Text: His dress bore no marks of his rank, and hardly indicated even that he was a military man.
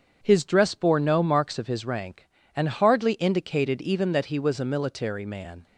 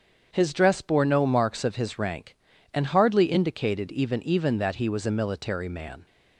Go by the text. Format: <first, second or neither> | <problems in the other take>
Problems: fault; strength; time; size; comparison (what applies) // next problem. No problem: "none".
first | starts louder than the rest; strong; until 1.3 s; 7.5 dB; strong in the first // says "even" twice; at 4.2 s